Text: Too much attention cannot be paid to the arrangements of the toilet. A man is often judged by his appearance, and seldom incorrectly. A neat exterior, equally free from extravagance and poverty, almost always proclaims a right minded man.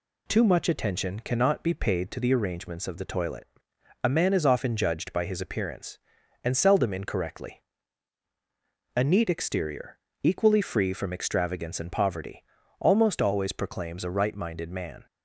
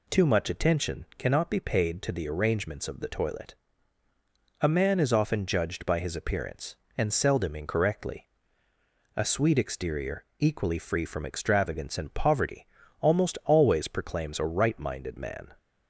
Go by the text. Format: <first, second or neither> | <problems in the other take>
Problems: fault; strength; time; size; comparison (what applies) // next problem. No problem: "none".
first | says "sweet" for "neat"; at 9.2 s